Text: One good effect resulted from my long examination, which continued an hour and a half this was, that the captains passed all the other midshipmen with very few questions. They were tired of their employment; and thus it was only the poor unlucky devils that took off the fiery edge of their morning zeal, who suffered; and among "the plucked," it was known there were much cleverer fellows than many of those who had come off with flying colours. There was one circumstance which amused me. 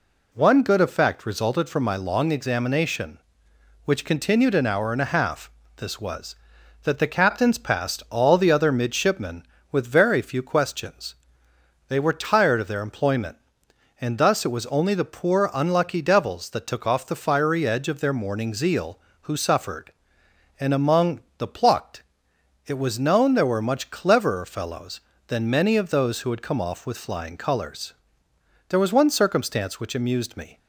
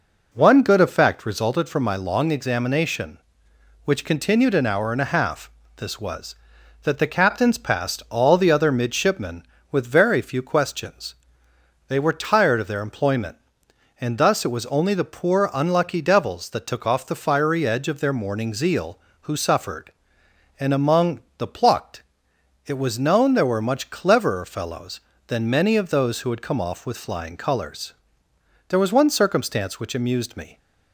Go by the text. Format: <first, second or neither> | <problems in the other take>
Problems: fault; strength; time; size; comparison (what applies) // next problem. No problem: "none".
first | starts louder than the rest; noticeable; until 1.4 s; 4.5 dB // pauses between "half" and "this"; slight; at 5.4 s; 0.26 s long; slight in the first // pauses between "among" and "the"; slight; at 21.1 s; 0.18 s long; slight in the first